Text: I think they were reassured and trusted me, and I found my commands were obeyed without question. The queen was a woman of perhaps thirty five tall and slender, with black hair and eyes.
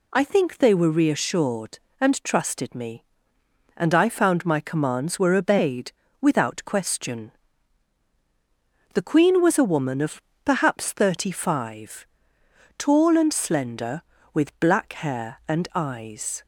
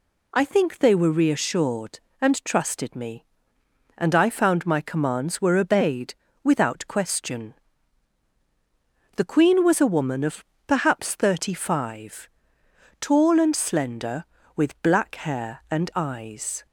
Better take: neither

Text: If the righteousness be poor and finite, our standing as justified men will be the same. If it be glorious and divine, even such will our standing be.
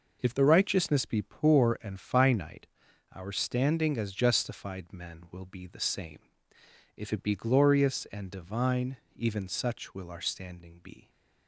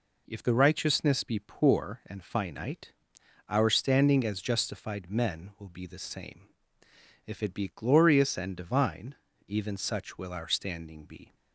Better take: neither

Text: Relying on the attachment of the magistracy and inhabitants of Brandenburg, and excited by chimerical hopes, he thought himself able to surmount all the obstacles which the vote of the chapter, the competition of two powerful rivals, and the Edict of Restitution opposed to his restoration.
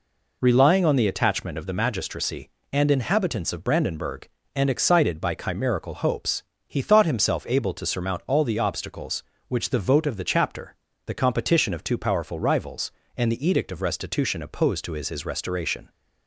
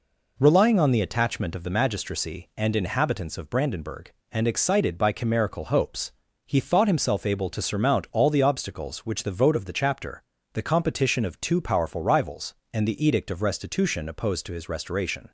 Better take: second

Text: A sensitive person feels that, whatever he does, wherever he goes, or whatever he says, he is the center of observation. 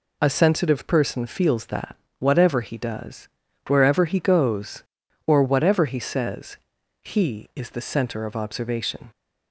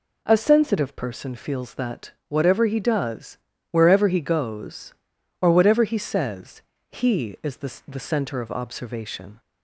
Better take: first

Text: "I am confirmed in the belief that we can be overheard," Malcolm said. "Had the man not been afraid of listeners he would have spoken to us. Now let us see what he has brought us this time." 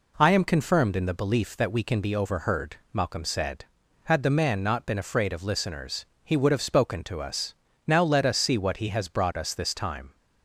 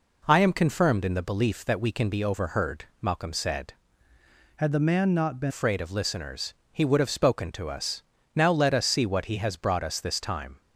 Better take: first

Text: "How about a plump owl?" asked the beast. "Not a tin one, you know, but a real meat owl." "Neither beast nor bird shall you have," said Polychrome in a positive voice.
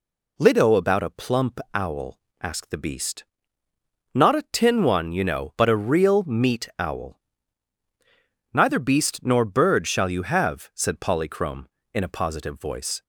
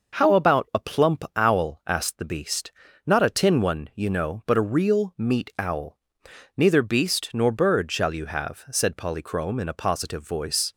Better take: second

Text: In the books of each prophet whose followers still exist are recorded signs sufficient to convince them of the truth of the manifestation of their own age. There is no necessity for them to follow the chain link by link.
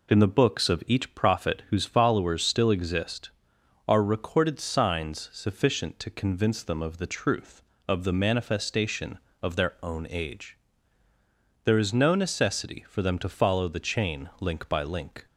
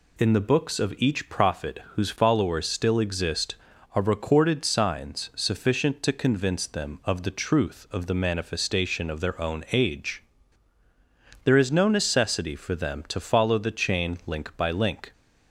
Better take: neither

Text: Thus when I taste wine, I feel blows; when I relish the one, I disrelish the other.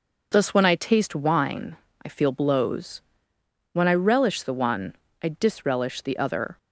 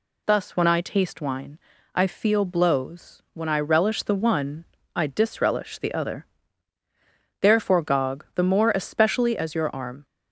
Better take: first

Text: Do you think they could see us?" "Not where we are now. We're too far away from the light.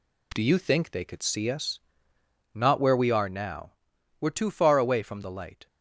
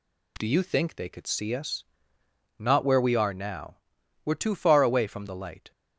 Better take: second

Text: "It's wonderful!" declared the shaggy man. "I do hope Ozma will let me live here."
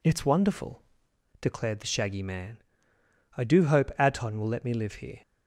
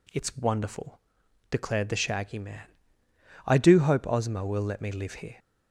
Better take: second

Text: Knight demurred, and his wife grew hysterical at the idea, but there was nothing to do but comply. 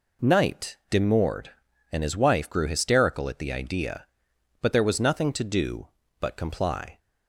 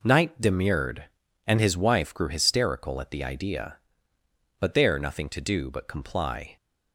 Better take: first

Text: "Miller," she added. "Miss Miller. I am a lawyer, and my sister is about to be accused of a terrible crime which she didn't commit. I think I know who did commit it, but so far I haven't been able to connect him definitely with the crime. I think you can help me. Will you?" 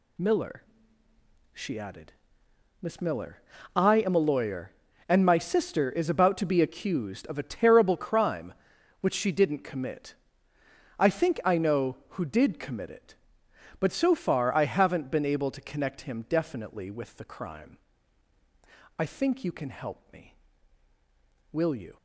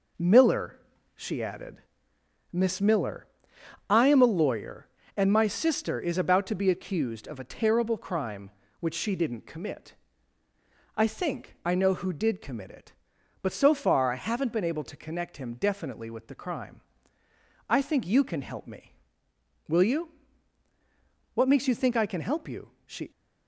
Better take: first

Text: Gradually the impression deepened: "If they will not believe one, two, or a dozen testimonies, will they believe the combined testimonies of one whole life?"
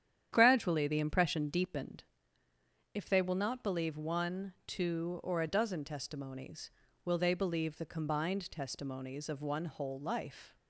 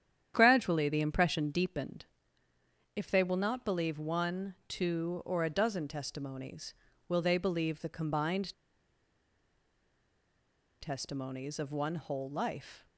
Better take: first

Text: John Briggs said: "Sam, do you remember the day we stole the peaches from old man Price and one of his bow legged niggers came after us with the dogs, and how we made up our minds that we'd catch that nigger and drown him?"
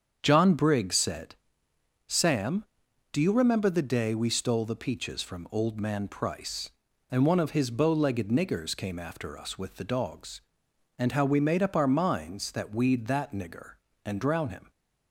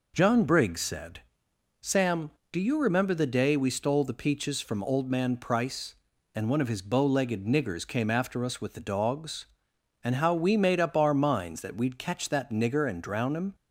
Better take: second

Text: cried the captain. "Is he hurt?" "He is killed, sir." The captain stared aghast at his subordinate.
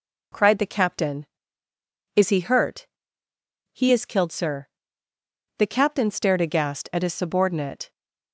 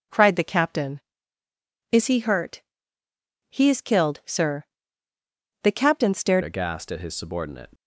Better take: first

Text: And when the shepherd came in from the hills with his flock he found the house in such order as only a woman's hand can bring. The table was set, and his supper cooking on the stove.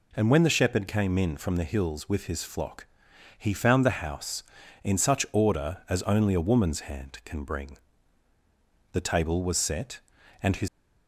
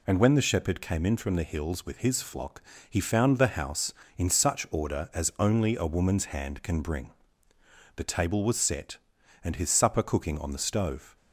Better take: second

